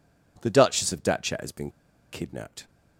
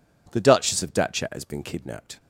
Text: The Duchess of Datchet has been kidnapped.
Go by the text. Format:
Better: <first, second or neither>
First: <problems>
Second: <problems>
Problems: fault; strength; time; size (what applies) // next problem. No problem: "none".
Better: second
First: pauses between "been" and "kidnapped"; at 1.7 s; 0.41 s long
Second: none